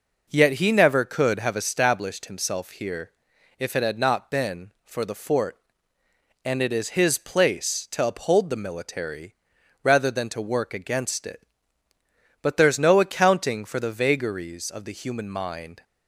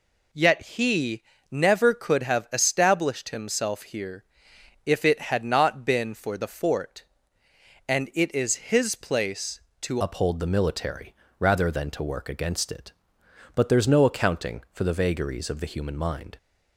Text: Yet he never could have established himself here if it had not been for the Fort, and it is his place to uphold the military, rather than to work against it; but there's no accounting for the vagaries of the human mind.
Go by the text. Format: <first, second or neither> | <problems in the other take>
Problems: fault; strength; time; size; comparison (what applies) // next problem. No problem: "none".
first | pauses between "he" and "never"; slight; at 1.2 s; 0.26 s long // pauses between "here" and "if"; noticeable; at 4.2 s; 0.62 s long; noticeable in the first // changes voice at "uphold"; from 9.9 s on; 6.4 s long